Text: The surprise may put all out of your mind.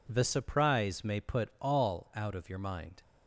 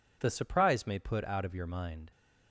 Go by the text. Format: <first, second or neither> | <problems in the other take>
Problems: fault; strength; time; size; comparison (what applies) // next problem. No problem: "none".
first | skips "all"; at 1.2 s